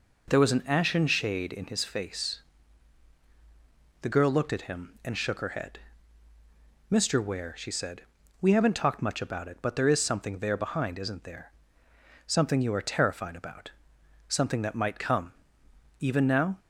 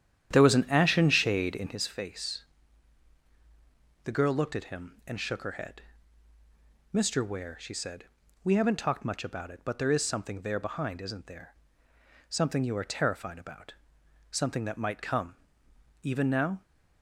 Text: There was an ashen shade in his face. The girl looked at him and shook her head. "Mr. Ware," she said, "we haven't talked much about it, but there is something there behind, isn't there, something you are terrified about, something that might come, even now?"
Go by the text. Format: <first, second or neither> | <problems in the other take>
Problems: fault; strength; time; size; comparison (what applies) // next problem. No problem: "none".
first | starts louder than the rest; strong; until 1.9 s; 10 dB